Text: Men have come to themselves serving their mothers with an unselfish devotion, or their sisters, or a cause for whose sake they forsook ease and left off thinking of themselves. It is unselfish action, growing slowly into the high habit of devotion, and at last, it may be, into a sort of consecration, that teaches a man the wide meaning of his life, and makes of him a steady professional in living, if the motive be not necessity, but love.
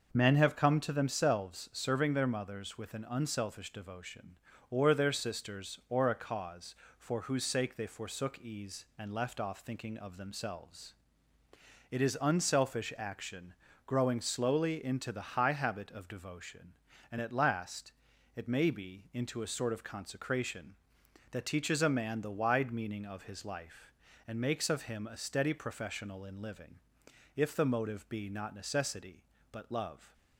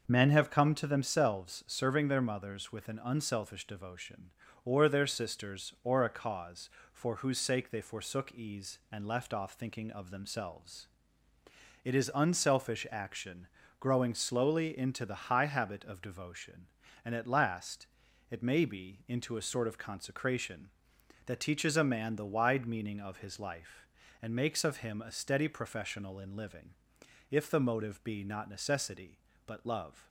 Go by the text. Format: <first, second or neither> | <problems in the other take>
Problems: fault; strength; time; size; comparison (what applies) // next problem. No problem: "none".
neither | starts louder than the rest; the same in both